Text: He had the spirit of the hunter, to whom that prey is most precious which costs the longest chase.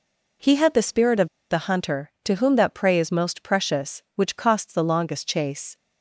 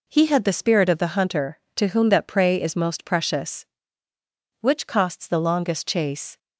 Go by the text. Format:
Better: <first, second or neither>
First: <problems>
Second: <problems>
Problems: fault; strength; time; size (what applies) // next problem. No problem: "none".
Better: second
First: pauses between "of" and "the"; slight; at 1.2 s; 0.22 s long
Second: none